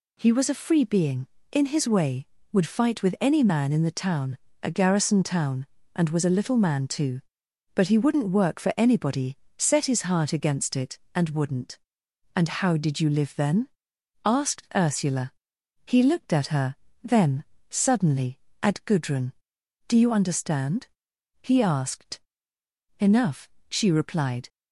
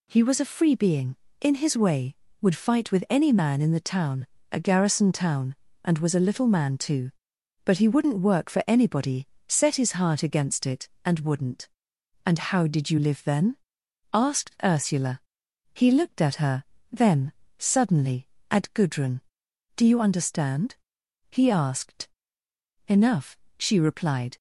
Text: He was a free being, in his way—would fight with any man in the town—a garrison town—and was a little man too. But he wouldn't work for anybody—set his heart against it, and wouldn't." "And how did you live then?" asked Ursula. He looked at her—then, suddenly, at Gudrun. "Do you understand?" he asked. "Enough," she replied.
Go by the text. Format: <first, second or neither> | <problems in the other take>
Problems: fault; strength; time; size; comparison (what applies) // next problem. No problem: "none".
neither | none